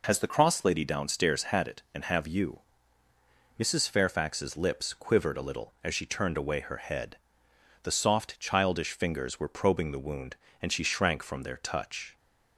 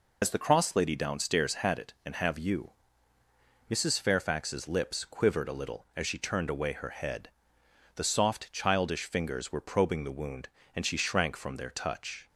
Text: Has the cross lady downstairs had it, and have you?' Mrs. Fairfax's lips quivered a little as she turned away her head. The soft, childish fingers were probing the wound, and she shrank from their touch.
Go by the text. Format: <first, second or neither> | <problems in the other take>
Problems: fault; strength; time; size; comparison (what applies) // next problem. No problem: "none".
first | loses the start of "Has"; at 0.2 s; 65 ms